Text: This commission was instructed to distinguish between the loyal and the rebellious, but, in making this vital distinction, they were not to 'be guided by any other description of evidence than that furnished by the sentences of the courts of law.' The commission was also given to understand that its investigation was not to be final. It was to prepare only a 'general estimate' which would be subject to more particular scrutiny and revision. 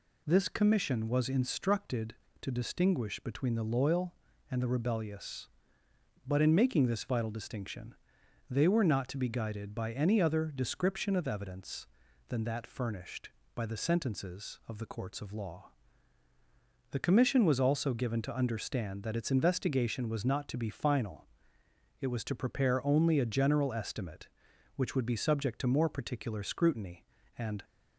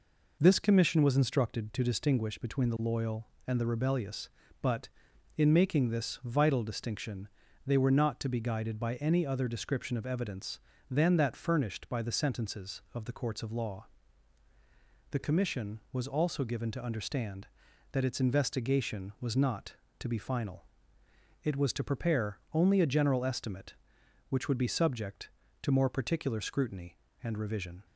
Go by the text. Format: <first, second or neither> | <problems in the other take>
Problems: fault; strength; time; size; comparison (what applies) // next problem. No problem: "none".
second | stops before "revision"; at 27.6 s